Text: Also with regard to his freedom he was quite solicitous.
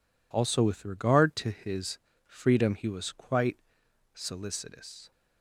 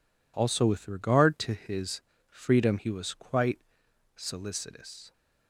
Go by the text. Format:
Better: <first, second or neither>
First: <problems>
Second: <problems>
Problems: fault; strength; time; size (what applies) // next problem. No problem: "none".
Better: neither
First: pauses between "his" and "freedom"; slight; at 1.9 s; 0.28 s long // pauses between "quite" and "solicitous"; noticeable; at 3.5 s; 0.58 s long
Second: pauses between "his" and "freedom"; slight; at 2.0 s; 0.28 s long // pauses between "quite" and "solicitous"; noticeable; at 3.5 s; 0.58 s long